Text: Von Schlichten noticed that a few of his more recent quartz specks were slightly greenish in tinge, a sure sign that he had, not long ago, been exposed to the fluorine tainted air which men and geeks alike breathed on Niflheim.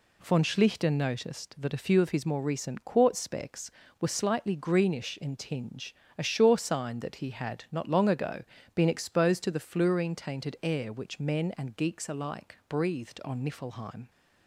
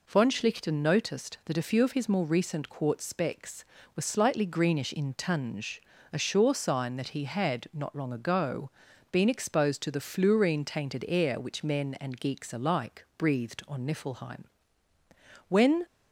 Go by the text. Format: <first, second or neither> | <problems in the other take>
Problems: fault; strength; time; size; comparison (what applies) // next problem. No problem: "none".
first | goes on to say "When"; slight; from 15.4 s on; 0.38 s long